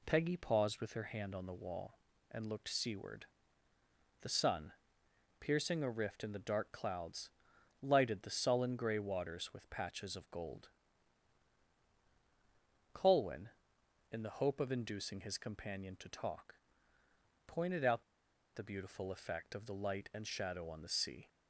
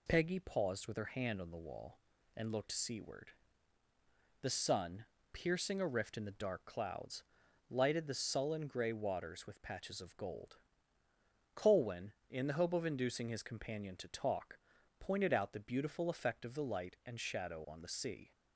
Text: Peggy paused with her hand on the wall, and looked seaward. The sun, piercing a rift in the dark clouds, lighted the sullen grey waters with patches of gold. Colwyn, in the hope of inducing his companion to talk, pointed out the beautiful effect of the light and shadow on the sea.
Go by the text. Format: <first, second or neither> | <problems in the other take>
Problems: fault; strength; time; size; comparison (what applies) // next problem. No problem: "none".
second | pauses between "out" and "the"; noticeable; at 18.0 s; 0.53 s long